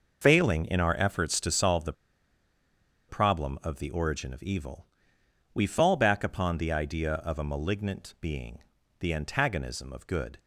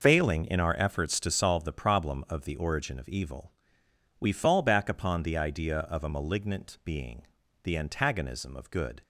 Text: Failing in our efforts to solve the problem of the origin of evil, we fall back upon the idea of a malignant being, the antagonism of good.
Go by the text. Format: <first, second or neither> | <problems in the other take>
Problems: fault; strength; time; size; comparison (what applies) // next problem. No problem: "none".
second | pauses between "the" and "problem"; at 1.9 s; 1.1 s long